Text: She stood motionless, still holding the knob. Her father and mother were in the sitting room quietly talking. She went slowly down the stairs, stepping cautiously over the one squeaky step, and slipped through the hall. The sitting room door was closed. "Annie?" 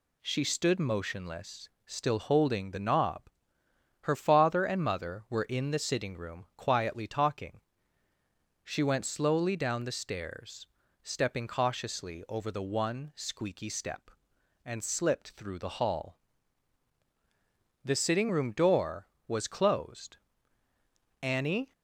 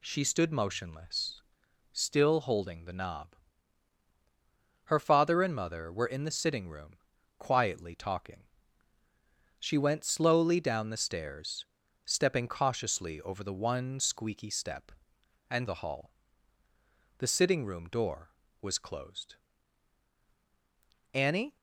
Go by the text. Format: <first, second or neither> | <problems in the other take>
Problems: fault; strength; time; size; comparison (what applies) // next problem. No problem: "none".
first | pauses between "room" and "quietly"; at 6.9 s; 0.44 s long // skips "slipped through"; at 15.6 s